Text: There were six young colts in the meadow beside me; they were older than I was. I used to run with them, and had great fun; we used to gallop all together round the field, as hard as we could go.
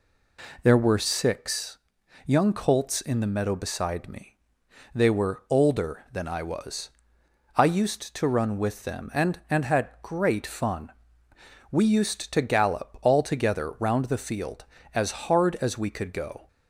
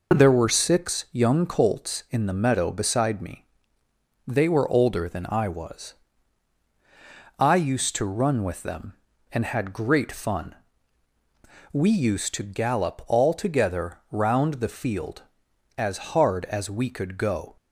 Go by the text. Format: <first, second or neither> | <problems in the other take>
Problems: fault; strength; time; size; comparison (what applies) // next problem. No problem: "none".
second | pauses between "six" and "young"; noticeable; at 1.7 s; 0.48 s long // says "and" twice; at 9.4 s